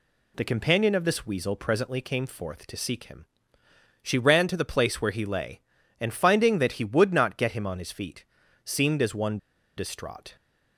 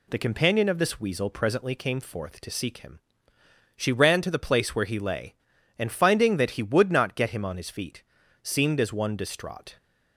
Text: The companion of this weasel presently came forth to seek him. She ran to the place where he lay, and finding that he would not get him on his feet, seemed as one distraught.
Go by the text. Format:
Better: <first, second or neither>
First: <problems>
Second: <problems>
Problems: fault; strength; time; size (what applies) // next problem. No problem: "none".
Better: second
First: pauses between "one" and "distraught"; at 9.3 s; 0.38 s long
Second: none